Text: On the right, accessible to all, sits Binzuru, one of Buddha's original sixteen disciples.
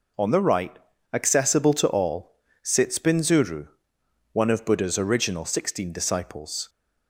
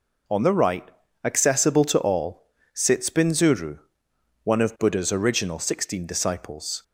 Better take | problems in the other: neither | none

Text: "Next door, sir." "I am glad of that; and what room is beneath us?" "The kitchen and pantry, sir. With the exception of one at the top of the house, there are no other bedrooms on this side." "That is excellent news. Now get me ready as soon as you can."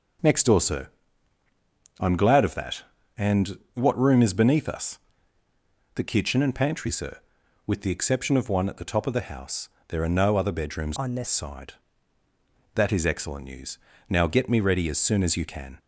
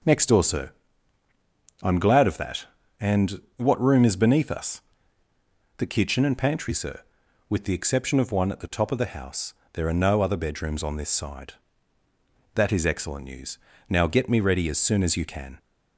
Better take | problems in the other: second | changes voice from "on" to "this"; from 10.9 to 11.2 s; 0.3 s long

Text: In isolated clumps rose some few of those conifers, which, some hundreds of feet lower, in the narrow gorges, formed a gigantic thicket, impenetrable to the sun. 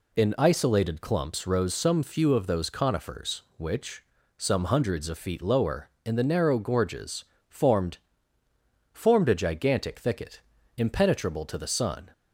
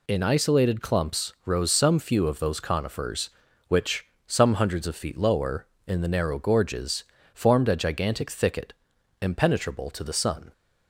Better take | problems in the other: second | says "formed" twice; at 8.9 s

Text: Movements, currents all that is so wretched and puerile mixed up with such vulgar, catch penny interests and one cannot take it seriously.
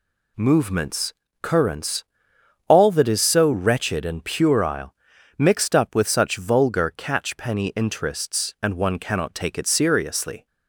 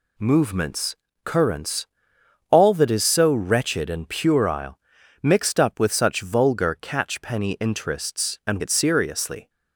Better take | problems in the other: first | pauses between "currents" and "all"; noticeable; at 1.8 s; 0.62 s long; noticeable in the first // pauses between "puerile" and "mixed"; at 4.7 s; 0.44 s long; also in the first // skips "one cannot take"; at 8.6 s

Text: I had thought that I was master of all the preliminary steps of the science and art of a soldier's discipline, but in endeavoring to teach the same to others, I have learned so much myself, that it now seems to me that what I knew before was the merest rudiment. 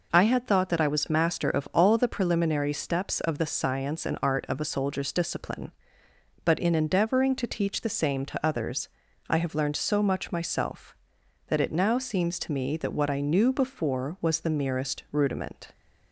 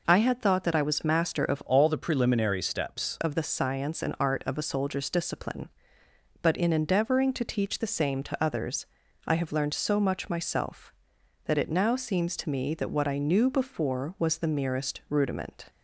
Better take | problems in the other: first | changes voice from "all" to "steps"; from 1.6 to 3.1 s; 1.5 s long

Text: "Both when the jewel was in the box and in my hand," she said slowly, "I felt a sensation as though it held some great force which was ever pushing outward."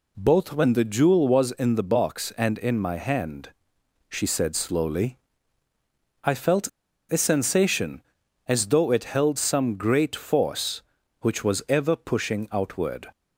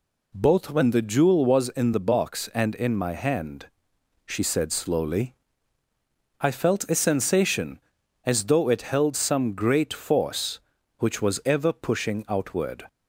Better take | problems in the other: second | pauses between "felt" and "a"; at 6.6 s; 0.42 s long

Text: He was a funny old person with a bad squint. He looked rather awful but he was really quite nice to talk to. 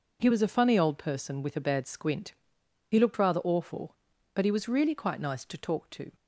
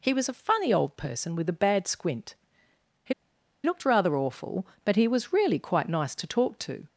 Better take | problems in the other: first | pauses between "He" and "looked"; noticeable; at 3.1 s; 0.51 s long

